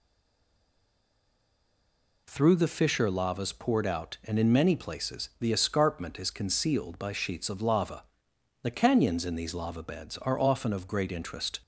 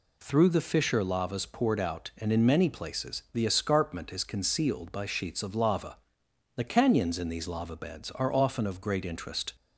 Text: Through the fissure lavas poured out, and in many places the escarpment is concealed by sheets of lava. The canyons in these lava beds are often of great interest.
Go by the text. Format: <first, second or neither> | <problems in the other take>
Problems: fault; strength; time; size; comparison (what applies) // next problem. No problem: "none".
second | stays silent before the first word; until 2.2 s; 2.2 s long